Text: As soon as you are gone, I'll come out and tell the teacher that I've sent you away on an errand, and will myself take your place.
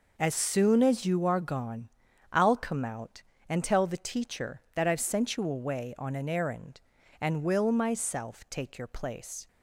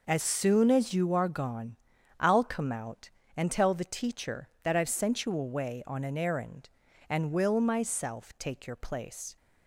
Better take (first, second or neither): neither